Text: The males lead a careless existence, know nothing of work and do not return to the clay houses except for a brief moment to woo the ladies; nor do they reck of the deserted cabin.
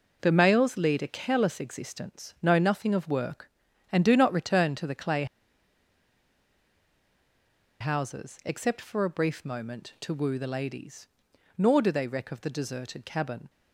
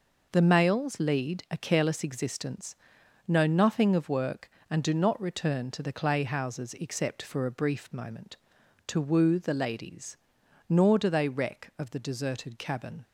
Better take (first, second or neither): second